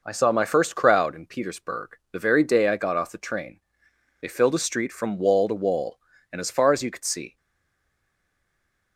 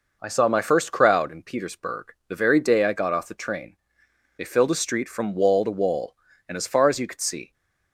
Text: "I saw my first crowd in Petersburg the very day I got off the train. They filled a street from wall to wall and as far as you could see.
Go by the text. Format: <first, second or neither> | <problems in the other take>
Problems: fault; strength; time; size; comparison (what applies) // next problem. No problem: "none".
second | stays silent after the last word; noticeable; from 7.3 s on; 1.6 s long